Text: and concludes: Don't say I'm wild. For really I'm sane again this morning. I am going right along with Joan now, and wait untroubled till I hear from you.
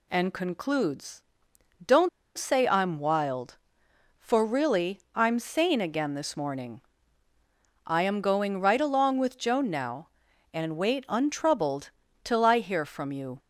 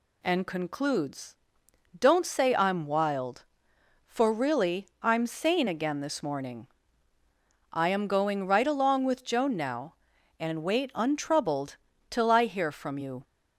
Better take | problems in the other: second | pauses between "Don't" and "say"; slight; at 2.0 s; 0.27 s long // pauses between "really" and "I'm"; slight; at 4.9 s; 0.16 s long; slight in the second // pauses between "untroubled" and "till"; slight; at 11.8 s; 0.36 s long; slight in the second

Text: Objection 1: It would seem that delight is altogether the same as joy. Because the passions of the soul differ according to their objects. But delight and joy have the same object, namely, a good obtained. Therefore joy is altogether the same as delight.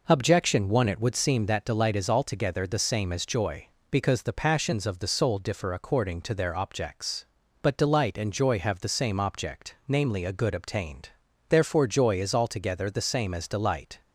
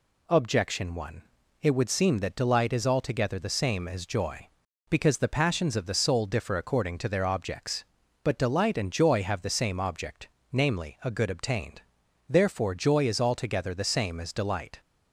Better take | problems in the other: neither | none

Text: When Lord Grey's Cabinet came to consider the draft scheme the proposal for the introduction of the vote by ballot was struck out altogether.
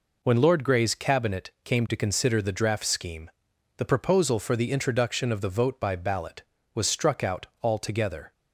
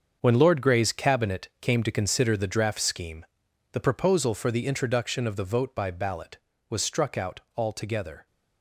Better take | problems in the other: first | gets quieter; strong; throughout; 11.5 dB // pauses between "scheme" and "the"; noticeable; at 3.2 s; 0.46 s long; noticeable in the first

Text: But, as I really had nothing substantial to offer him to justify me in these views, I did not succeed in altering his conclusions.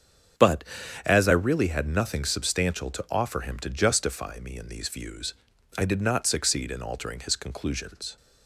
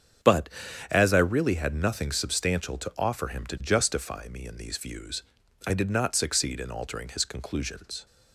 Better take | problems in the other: neither | starts louder than the rest; strong; the same in both

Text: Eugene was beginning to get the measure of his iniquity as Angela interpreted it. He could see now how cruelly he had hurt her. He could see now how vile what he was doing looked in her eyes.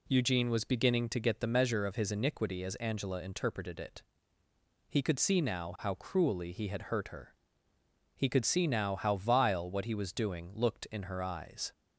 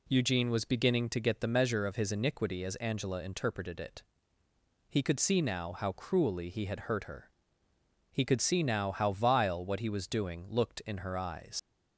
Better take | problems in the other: first | leaves "eyes" unfinished; at 11.5 s; 65 ms

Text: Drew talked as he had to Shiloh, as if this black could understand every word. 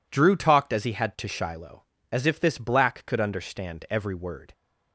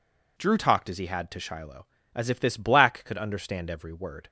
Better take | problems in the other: neither | none

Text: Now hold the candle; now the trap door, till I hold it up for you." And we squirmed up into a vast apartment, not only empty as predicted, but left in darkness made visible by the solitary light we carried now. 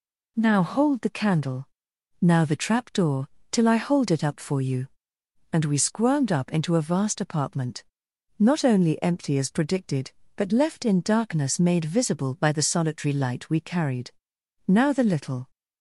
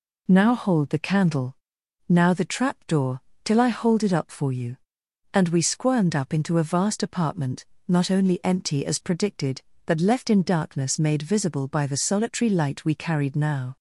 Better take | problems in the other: second | pauses between "carried" and "now"; noticeable; at 14.1 s; 0.56 s long // goes on to say "The little"; from 14.9 s on; 0.58 s long

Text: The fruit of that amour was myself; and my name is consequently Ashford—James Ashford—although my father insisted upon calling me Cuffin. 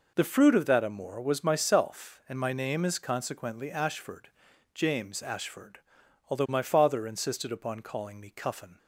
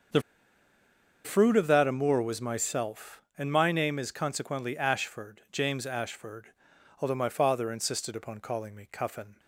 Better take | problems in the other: first | starts louder than the rest; until 2.1 s; 6.5 dB // pauses between "The" and "fruit"; at 0.2 s; 1.0 s long

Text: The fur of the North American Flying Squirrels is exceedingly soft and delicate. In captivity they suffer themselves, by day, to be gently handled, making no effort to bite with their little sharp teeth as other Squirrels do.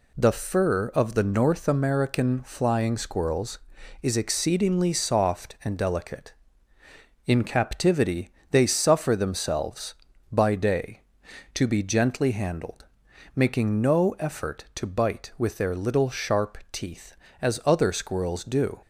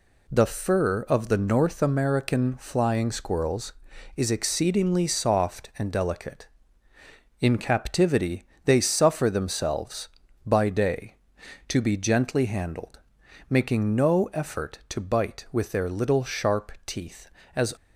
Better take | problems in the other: first | pauses between "captivity" and "they"; slight; at 8.4 s; 0.22 s long; slight in the first // stops before "other Squirrels do"; at 17.7 s

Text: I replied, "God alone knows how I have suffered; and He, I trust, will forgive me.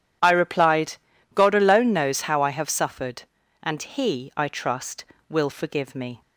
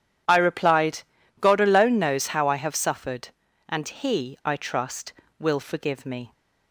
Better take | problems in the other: neither | none

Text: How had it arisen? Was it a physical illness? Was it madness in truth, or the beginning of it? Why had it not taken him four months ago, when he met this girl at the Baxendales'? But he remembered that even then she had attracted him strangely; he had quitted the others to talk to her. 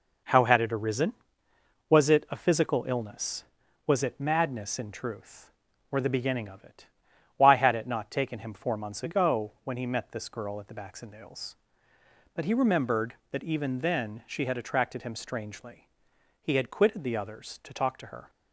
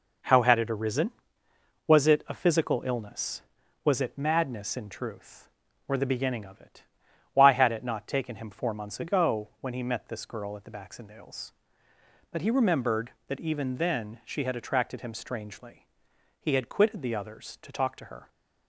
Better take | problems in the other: neither | none

